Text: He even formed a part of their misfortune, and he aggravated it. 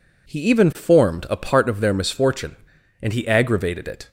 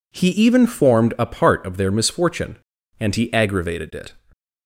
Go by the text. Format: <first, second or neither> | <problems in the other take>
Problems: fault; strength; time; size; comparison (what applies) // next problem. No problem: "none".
neither | none